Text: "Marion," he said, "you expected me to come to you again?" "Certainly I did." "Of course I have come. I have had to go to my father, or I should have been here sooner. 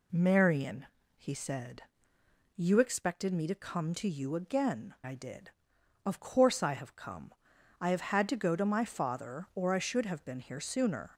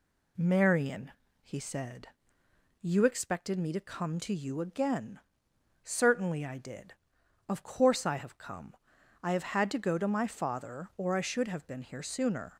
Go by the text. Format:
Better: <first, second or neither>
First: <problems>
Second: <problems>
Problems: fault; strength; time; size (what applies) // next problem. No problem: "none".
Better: second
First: skips "Certainly"; at 4.9 s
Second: none